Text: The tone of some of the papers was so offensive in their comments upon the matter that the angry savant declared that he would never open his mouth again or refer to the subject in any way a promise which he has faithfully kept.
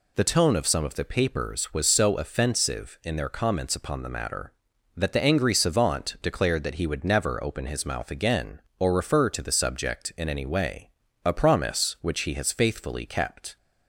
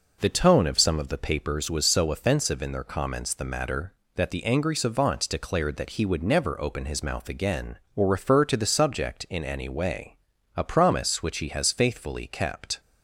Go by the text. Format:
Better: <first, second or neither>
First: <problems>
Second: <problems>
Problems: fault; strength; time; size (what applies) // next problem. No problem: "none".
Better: first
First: pauses between "way" and "a"; slight; at 10.9 s; 0.34 s long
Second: skips "upon"; at 3.3 s // pauses between "way" and "a"; at 10.1 s; 0.40 s long